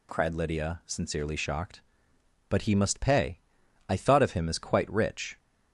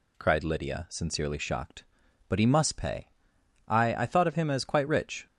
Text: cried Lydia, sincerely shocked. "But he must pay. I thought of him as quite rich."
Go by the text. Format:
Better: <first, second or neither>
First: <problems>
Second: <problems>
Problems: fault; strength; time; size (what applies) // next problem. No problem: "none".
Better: first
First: none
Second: says "I" twice; at 3.9 s